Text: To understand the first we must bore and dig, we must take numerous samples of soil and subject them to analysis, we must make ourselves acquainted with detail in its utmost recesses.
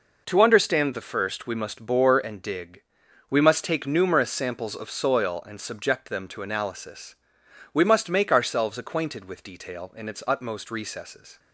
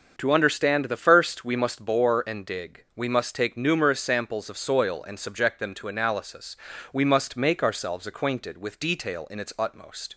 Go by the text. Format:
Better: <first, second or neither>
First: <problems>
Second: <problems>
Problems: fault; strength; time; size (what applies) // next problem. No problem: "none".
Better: first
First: none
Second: starts louder than the rest; until 1.1 s; 7 dB // stops before "recesses"; at 10.1 s